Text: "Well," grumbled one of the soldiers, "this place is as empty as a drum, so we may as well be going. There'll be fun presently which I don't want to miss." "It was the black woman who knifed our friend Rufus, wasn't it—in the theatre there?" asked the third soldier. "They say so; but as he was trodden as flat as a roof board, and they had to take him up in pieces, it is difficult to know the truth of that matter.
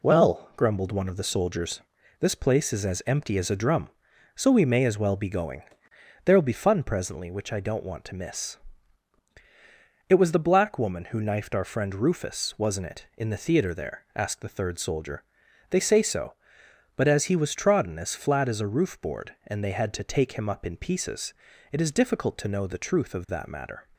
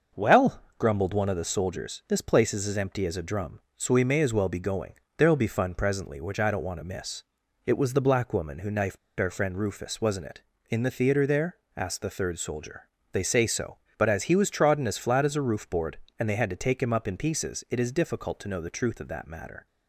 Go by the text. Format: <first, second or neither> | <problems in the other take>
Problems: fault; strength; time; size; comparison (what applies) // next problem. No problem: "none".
first | starts louder than the rest; until 1.3 s; 6 dB // pauses between "knifed" and "our"; slight; at 8.9 s; 0.21 s long